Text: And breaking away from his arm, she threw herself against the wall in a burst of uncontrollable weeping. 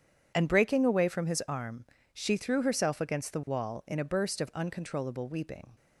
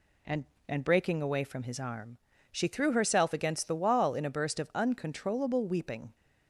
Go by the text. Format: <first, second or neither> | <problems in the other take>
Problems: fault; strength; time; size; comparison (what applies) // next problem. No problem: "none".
first | says "And" twice; at 0.6 s